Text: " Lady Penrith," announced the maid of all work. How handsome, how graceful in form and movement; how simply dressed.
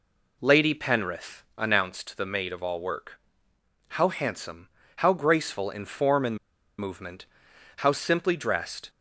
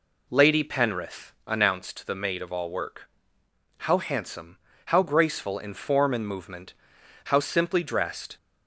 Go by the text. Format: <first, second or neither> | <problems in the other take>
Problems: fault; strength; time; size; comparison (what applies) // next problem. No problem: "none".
second | pauses between "and" and "movement"; at 6.3 s; 0.41 s long